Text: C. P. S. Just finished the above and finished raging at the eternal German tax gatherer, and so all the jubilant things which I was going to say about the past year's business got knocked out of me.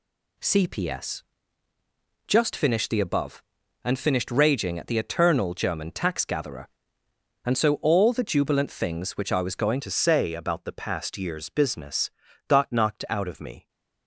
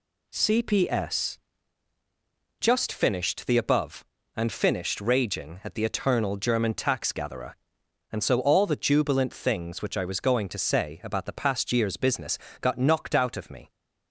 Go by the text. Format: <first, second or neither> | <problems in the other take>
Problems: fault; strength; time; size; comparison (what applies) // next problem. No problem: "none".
second | changes voice at "to"; from 9.8 s on; 3.8 s long // pauses between "business" and "got"; at 12.0 s; 0.38 s long; slight in the second